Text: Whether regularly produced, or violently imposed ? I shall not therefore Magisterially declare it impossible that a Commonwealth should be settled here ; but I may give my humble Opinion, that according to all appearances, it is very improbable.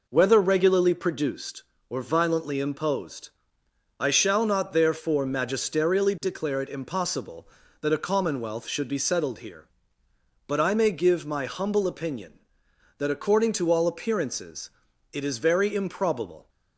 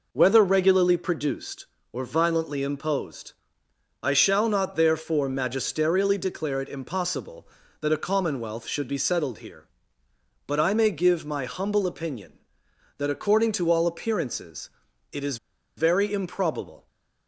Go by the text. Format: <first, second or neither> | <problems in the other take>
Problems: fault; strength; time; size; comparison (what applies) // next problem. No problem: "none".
first | pauses between "is" and "very"; at 15.3 s; 0.40 s long